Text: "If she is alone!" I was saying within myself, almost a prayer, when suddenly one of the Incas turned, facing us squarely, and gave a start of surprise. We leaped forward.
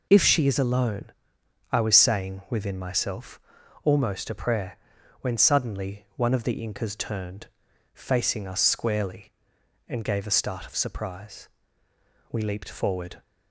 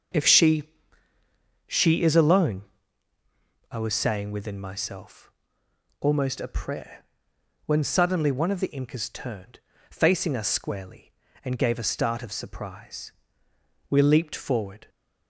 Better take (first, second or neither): first